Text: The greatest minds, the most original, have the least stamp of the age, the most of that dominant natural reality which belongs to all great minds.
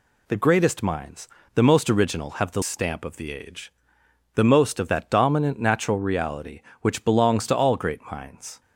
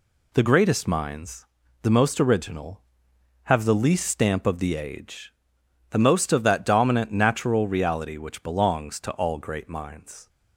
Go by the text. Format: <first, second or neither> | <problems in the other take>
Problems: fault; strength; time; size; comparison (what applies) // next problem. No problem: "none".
second | skips "least"; at 2.6 s